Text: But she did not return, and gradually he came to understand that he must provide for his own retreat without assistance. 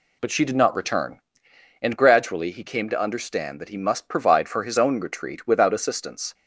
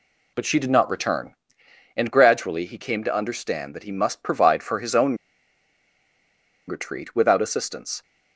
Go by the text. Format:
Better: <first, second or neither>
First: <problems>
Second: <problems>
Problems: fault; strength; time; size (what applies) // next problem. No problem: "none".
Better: first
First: none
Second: pauses between "own" and "retreat"; strong; at 5.1 s; 1.5 s long